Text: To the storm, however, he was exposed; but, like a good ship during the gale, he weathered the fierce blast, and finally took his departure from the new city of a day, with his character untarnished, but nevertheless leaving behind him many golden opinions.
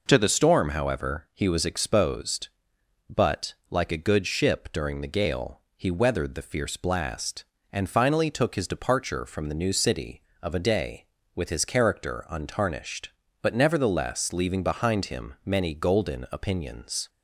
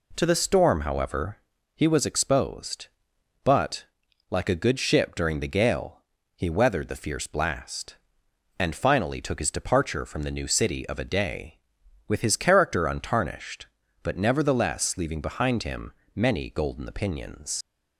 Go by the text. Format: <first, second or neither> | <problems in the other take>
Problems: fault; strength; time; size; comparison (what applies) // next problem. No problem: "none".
first | pauses between "him" and "many"; slight; at 15.9 s; 0.22 s long // leaves "opinions" unfinished; at 17.6 s; 130 ms